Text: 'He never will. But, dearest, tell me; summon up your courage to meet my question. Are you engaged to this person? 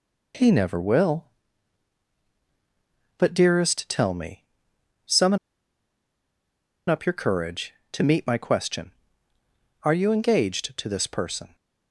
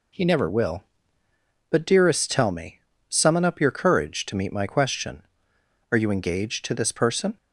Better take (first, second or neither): second